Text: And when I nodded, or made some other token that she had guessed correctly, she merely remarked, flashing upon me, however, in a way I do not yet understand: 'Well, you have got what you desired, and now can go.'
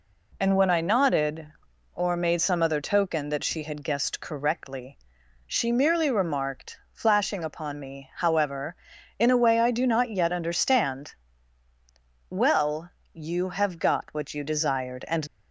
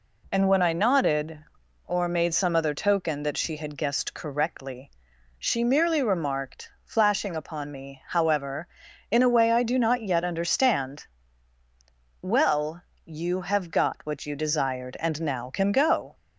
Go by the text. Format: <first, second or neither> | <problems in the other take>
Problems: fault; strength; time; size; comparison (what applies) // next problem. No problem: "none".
second | stops before "now can go"; at 15.2 s